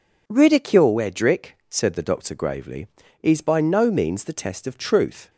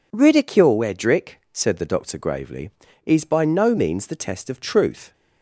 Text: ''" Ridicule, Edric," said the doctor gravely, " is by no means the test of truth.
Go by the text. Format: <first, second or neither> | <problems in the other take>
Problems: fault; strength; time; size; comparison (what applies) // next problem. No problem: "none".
neither | none